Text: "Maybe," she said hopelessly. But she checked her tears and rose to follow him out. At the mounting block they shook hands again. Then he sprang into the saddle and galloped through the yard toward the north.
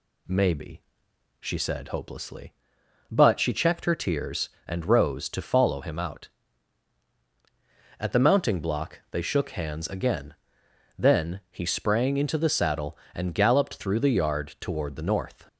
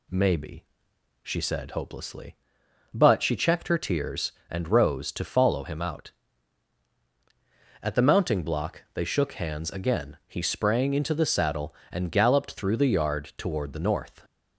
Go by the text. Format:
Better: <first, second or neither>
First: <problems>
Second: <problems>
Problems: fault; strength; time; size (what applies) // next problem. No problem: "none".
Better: first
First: none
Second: skips "Then"; at 10.2 s